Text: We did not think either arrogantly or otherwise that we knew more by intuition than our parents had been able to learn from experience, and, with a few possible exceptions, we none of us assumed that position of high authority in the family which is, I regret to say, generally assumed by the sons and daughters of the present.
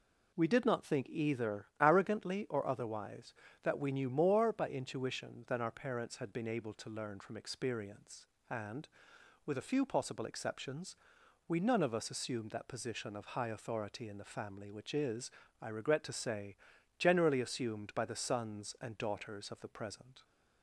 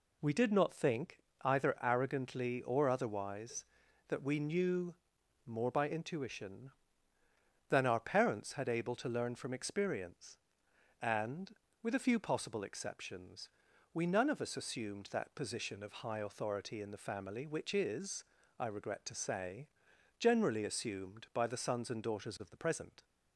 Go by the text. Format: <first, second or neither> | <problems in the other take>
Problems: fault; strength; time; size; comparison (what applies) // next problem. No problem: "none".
first | pauses between "think" and "either"; slight; at 1.1 s; 0.24 s long // pauses between "knew" and "more"; noticeable; at 4.9 s; 0.50 s long // skips "been"; at 8.6 s